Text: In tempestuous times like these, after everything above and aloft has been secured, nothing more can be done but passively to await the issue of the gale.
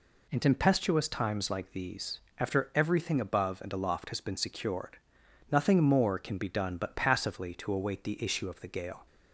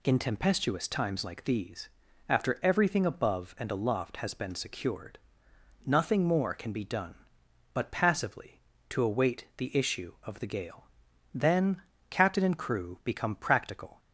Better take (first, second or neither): first